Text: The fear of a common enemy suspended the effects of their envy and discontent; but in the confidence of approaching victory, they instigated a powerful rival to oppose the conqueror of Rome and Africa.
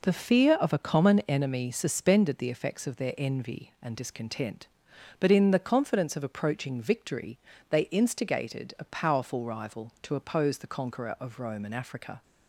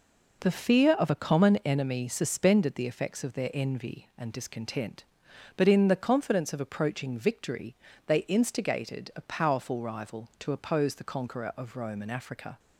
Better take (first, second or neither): neither